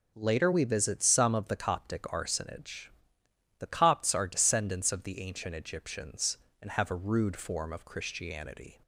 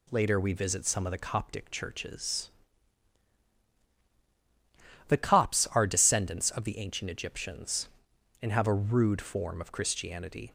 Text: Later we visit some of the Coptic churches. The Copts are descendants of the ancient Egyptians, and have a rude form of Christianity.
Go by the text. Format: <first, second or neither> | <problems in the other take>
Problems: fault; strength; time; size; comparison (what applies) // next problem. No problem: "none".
second | says "arsonage" for "churches"; at 2.0 s